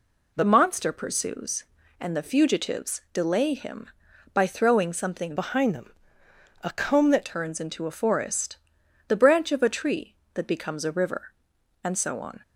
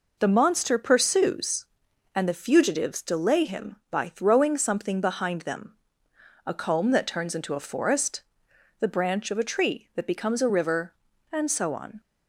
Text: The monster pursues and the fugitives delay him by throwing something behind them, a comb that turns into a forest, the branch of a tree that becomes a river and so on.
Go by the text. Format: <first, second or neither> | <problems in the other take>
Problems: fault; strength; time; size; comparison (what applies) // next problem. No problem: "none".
second | changes voice from "behind" to "that"; from 5.3 to 7.2 s; 1.9 s long